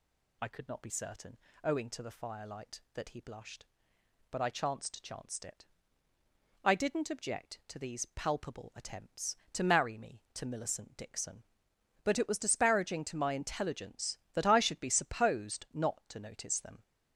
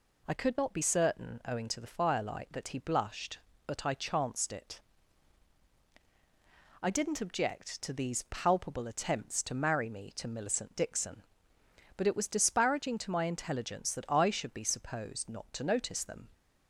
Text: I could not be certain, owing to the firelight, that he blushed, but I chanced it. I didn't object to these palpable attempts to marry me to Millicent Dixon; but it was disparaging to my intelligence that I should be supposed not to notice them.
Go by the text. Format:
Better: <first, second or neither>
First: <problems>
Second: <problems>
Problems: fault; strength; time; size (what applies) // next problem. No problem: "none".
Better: second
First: says "chanced" twice; at 5.0 s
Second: none